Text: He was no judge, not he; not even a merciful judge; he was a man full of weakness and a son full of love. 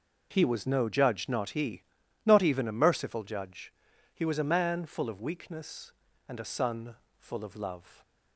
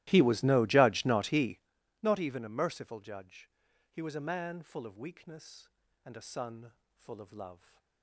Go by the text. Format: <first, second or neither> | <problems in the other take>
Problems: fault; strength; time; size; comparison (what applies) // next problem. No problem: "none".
first | starts louder than the rest; strong; until 1.6 s; 16.5 dB // pauses between "son" and "full"; slight; at 6.7 s; 0.22 s long; slight in the first